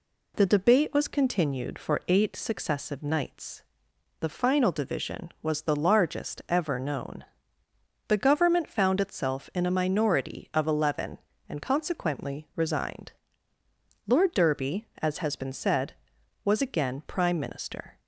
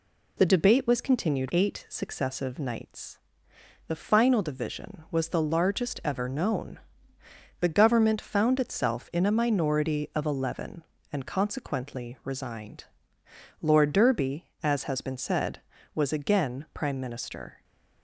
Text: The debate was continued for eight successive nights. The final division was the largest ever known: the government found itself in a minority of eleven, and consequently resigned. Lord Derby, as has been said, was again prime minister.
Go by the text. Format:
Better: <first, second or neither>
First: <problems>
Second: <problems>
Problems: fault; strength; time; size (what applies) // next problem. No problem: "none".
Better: first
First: none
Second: skips "for"; at 1.4 s